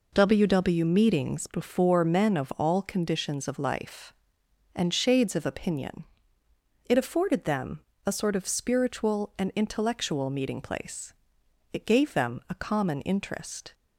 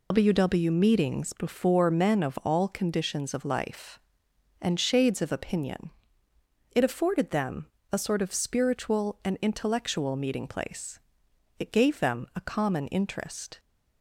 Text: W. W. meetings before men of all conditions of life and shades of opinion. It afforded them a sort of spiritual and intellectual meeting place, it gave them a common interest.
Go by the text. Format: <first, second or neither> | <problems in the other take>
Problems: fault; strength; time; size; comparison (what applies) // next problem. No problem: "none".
first | loses the start of "W"; at 0.1 s; 115 ms // pauses between "them" and "a"; slight; at 7.6 s; 0.26 s long; slight in the first